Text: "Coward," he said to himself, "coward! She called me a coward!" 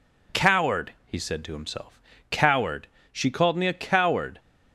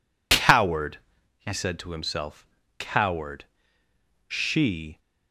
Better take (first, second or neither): first